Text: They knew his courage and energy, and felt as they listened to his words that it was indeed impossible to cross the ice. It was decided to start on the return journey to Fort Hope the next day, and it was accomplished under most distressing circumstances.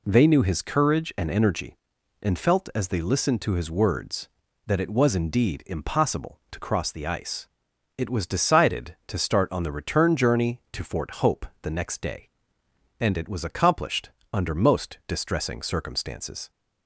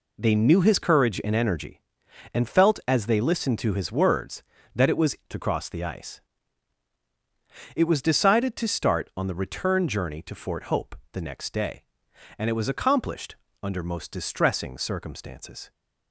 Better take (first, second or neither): first